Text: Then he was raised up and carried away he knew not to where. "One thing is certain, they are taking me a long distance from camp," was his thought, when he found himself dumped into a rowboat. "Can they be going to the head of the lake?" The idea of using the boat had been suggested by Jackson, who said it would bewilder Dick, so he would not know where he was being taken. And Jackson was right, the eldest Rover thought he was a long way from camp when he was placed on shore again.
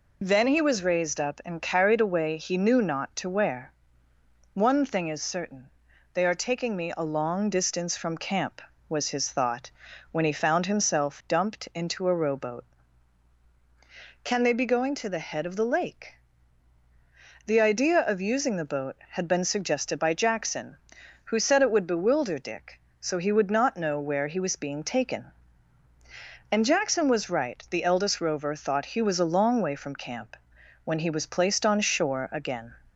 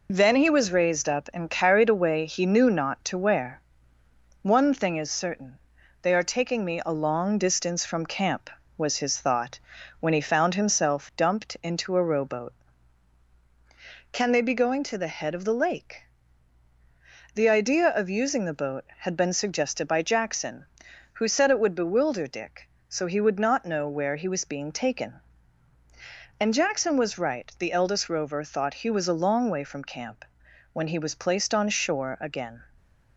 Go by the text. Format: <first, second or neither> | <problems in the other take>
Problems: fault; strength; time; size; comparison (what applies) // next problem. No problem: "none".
first | gets quieter; noticeable; throughout; 4.5 dB // pauses between "camp" and "when"; noticeable; at 30.2 s; 0.48 s long; noticeable in the first